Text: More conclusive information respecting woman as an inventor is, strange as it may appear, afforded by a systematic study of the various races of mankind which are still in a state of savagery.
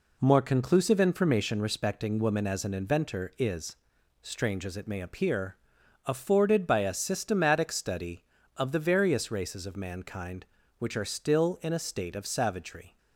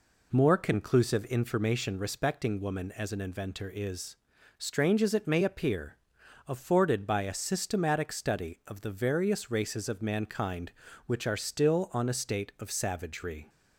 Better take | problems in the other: first | says "on" for "in"; at 11.9 s

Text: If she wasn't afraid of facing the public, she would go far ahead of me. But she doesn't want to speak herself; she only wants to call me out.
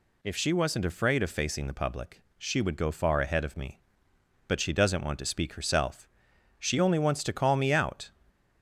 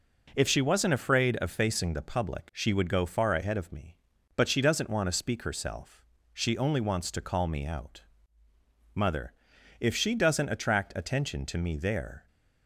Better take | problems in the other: first | goes on to say "Mother if she doesn't attract attention to me there"; strong; from 8.9 s on; 3.3 s long

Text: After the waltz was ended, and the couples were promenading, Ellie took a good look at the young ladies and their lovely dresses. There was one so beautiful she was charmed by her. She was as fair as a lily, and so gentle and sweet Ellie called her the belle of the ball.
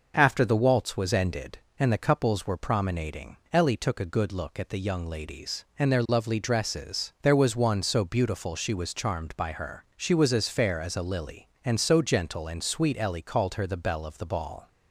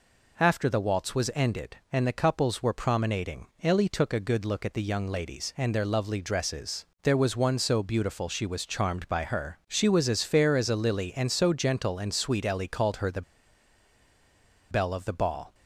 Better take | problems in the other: first | pauses between "the" and "belle"; strong; at 13.2 s; 1.4 s long

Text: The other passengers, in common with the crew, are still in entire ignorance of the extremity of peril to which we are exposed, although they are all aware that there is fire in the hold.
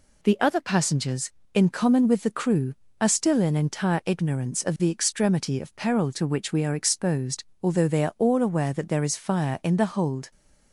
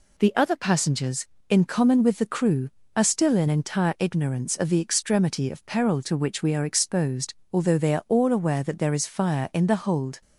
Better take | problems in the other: neither | none

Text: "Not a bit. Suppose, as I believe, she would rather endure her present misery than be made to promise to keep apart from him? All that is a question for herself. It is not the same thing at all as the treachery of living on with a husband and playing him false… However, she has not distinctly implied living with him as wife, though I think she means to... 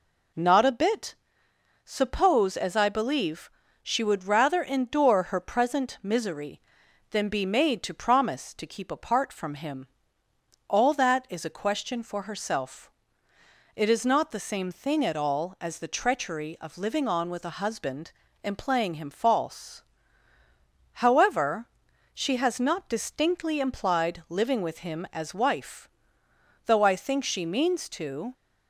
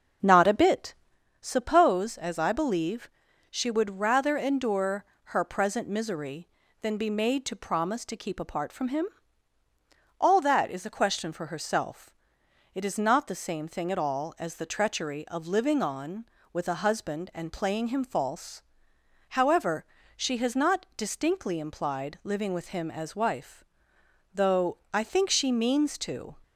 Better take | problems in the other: first | starts louder than the rest; noticeable; until 1.2 s; 6 dB // pauses between "endure" and "her"; slight; at 5.0 s; 0.20 s long

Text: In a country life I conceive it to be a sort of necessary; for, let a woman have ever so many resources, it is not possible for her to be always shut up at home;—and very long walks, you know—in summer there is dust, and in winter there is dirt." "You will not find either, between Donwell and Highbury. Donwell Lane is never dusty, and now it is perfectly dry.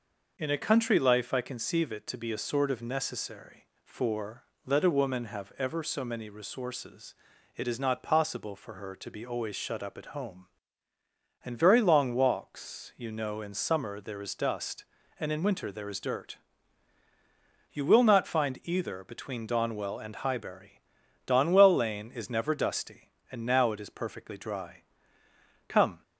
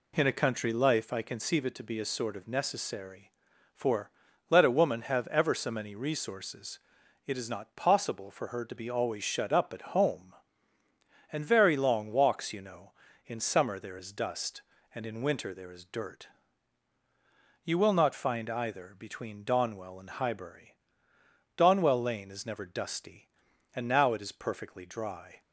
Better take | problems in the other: second | goes on to say "Come"; slight; from 25.6 s on; 0.34 s long

